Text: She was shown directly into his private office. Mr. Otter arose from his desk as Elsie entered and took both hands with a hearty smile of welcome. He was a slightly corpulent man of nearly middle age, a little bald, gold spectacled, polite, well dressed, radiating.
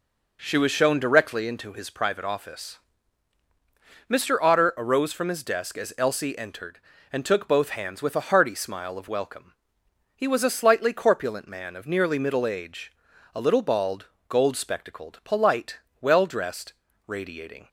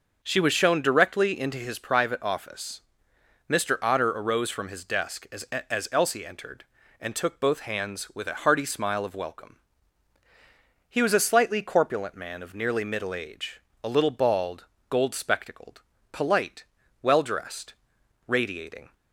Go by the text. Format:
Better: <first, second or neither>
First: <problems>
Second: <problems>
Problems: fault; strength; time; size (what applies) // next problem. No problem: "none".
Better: first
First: none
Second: starts louder than the rest; noticeable; until 1.2 s; 6 dB // says "as" twice; at 5.4 s